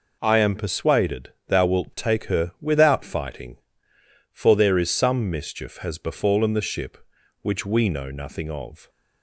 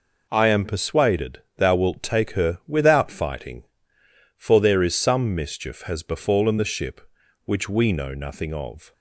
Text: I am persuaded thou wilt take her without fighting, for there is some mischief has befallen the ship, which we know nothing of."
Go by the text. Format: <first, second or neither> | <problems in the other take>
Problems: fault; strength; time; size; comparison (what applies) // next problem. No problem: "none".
neither | pauses between "persuaded" and "thou"; slight; the same in both